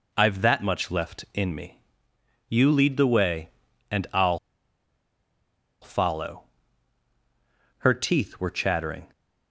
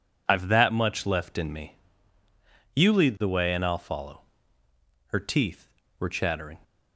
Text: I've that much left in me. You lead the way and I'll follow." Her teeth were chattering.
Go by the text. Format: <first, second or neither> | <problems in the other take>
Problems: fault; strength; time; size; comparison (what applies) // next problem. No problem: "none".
second | pauses between "I'll" and "follow"; strong; at 4.3 s; 1.4 s long